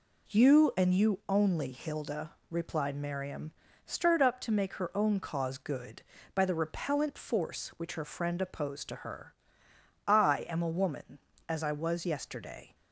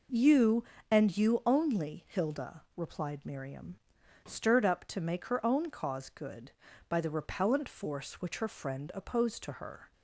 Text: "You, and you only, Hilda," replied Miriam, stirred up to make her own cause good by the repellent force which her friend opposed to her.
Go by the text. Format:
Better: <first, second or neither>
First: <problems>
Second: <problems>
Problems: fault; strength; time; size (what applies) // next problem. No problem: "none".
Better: second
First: goes on to say "I am a woman as I was yesterday"; strong; from 10.0 s on; 2.7 s long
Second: none